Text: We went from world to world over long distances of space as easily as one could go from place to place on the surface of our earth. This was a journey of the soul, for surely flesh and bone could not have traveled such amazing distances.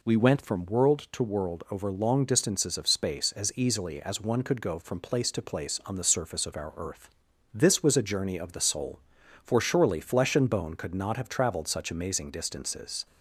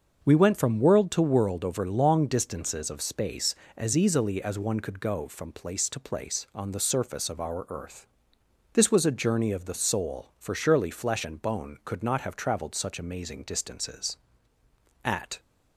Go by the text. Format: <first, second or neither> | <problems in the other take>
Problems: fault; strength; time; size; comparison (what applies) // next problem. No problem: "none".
first | starts louder than the rest; until 1.2 s; 6.5 dB // goes on to say "At"; slight; from 15.0 s on; 0.34 s long